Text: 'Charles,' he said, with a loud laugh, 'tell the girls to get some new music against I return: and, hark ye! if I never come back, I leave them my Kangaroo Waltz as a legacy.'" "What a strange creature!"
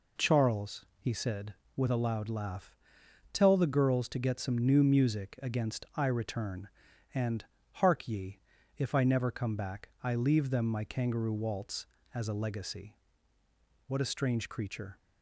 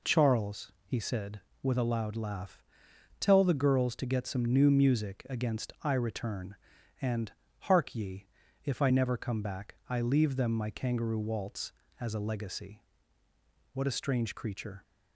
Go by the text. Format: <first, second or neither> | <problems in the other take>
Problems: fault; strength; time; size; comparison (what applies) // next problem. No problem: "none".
neither | none